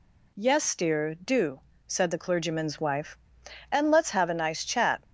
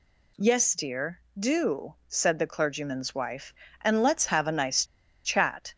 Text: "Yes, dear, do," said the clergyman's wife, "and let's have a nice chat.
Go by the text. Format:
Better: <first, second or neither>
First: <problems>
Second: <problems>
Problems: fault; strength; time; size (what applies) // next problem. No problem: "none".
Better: first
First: none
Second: pauses between "nice" and "chat"; at 4.8 s; 0.41 s long